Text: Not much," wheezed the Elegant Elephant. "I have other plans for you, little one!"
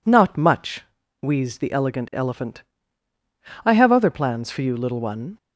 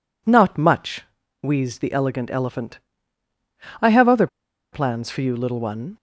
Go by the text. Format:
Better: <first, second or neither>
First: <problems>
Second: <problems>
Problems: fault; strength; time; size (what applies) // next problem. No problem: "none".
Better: first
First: none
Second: pauses between "other" and "plans"; at 4.2 s; 0.45 s long